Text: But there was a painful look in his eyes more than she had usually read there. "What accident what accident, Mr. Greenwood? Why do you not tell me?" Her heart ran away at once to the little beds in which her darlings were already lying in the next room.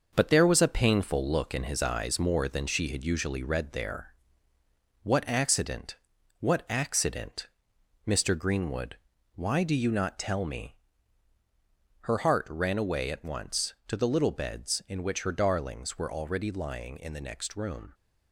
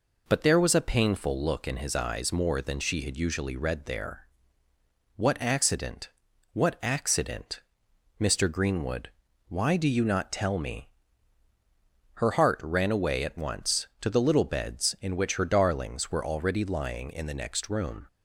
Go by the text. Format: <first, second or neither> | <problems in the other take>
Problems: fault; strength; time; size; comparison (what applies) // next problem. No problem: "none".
second | gets quieter; throughout; 6.5 dB // pauses between "accident" and "what"; at 5.9 s; 0.44 s long; also in the second